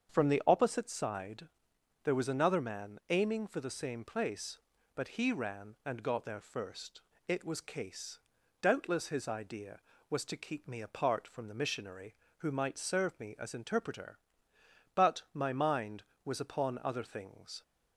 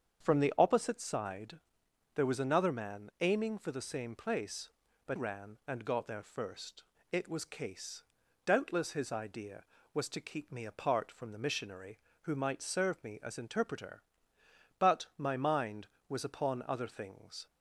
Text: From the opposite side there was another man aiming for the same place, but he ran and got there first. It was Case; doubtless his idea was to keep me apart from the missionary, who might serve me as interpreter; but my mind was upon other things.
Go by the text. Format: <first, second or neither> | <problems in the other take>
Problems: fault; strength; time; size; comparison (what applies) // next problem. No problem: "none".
first | starts louder than the rest; strong; until 1.2 s; 7.5 dB; strong in the first // pauses between "side" and "there"; noticeable; at 1.5 s; 0.56 s long; noticeable in the first // skips "he"; at 5.1 s